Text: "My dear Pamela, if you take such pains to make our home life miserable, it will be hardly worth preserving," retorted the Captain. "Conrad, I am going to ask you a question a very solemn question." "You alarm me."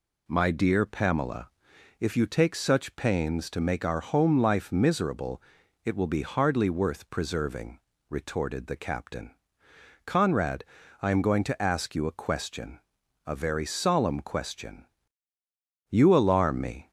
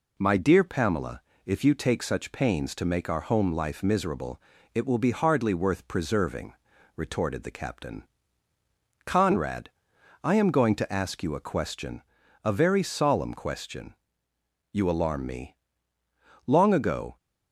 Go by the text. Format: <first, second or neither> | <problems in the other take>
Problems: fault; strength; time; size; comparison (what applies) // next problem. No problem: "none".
first | pauses between "question" and "a"; at 12.0 s; 0.44 s long; also in the first // goes on to say "Long ago"; noticeable; from 16.4 s on; 0.70 s long